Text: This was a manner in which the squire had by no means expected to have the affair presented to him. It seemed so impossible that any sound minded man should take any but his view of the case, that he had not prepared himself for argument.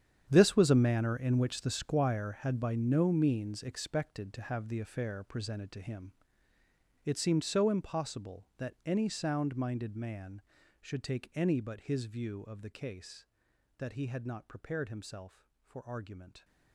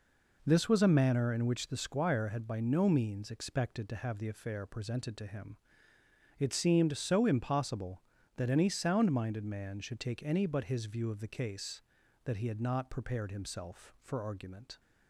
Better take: second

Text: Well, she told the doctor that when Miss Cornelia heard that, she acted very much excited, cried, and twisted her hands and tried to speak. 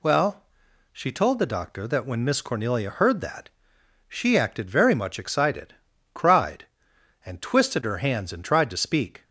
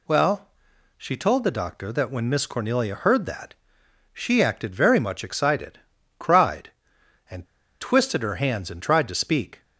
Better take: first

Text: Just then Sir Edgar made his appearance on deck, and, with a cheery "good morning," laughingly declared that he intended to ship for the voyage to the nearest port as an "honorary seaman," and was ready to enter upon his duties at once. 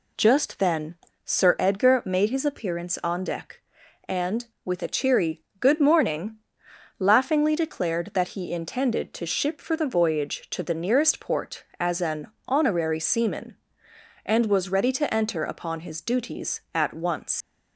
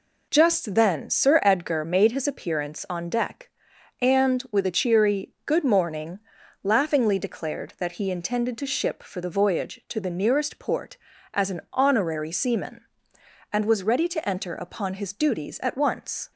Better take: second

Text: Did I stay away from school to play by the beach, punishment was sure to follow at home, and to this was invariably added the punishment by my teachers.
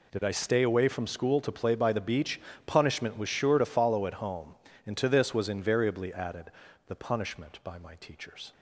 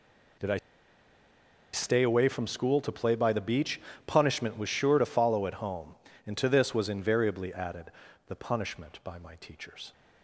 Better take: first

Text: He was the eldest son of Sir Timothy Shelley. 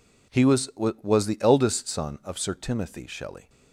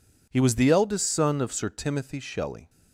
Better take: second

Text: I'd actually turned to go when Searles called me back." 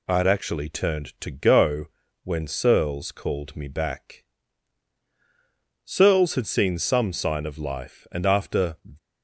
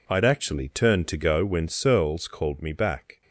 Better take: second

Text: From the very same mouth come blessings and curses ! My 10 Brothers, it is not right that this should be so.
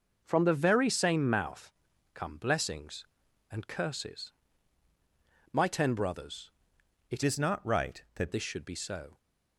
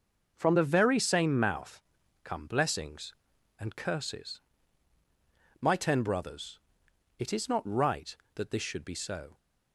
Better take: second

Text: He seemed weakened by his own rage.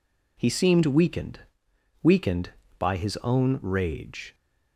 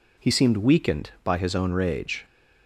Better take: second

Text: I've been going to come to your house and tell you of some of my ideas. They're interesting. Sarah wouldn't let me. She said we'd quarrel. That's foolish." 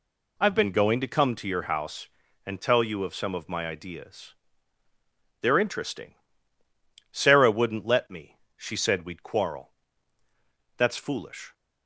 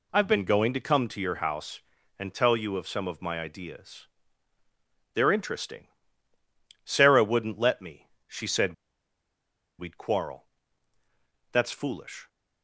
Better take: first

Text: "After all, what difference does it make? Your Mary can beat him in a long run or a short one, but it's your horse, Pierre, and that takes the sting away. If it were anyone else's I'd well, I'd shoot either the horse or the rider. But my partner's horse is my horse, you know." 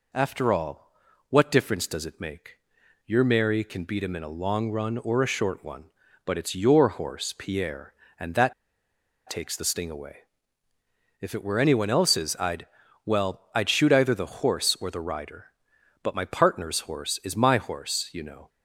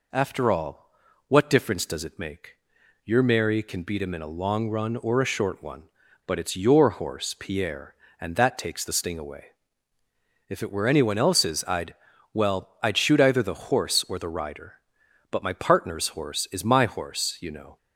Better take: second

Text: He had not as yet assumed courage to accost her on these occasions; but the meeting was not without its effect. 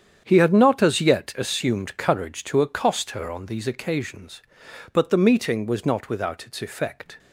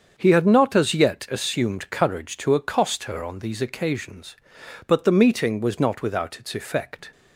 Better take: second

